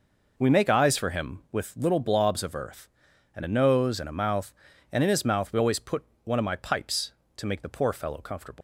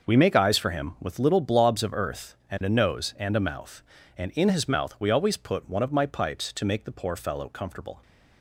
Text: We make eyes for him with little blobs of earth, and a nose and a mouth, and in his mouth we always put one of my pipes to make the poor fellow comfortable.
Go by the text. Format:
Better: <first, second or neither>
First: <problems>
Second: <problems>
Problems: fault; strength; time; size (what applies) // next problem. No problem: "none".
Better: second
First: pauses between "put" and "one"; slight; at 6.0 s; 0.20 s long // leaves "comfortable" unfinished; at 8.5 s; 145 ms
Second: none